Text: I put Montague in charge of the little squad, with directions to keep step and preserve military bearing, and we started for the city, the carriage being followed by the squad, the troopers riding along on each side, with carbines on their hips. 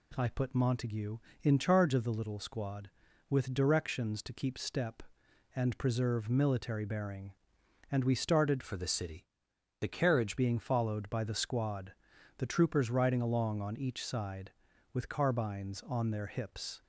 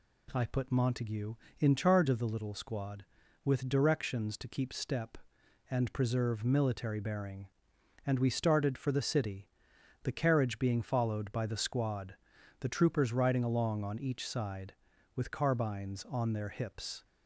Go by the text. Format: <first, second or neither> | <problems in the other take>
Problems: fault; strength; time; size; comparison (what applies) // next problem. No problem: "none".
second | changes voice from "for" to "carriage"; from 8.6 to 10.3 s; 1.7 s long